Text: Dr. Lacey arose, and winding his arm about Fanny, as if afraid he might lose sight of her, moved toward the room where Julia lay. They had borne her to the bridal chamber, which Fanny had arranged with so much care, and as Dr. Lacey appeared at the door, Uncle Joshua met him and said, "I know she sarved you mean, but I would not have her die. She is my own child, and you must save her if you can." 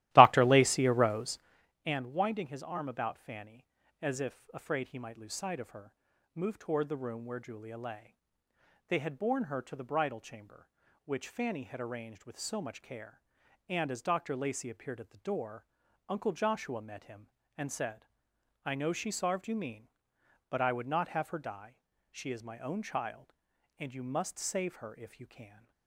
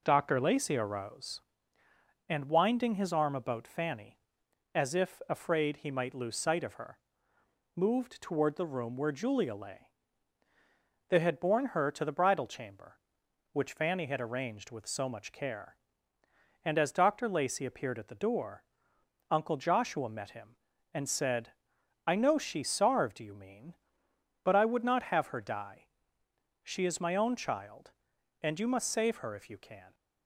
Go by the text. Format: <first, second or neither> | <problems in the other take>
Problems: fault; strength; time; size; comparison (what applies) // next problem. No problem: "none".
second | starts louder than the rest; strong; until 1.6 s; 15.5 dB